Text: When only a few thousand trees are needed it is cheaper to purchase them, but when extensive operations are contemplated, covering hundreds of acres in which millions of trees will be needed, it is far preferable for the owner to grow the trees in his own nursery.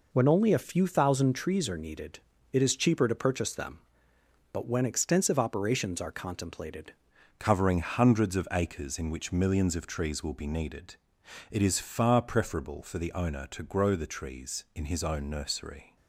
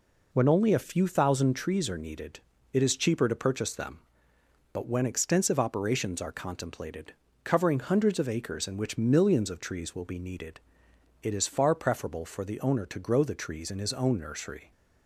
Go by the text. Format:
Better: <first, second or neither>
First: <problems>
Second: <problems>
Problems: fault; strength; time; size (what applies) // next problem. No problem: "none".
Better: second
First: pauses between "needed" and "it"; slight; at 2.1 s; 0.34 s long // changes voice at "covering"; from 7.3 s on; 8.6 s long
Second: pauses between "needed" and "it"; slight; at 2.3 s; 0.34 s long